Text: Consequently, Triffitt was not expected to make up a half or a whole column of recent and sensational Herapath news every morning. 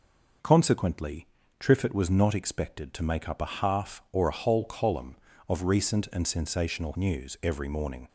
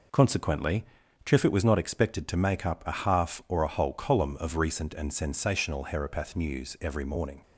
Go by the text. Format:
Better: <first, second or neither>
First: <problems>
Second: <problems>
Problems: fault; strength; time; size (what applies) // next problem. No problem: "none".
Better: second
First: skips "Herapath"; at 6.9 s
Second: none